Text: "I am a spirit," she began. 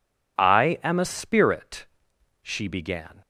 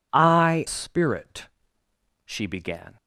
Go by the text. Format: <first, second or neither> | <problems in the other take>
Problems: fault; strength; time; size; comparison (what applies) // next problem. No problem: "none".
first | skips "am a"; at 0.6 s